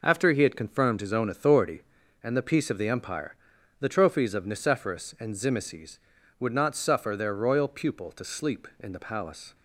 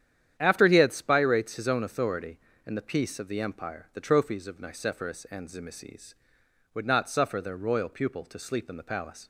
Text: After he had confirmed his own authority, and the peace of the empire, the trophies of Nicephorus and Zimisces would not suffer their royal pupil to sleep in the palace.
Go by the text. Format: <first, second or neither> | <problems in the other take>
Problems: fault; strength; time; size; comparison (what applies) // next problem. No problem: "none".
first | starts louder than the rest; strong; until 1.3 s; 9.5 dB // says "spirates" for "confirmed"; at 0.9 s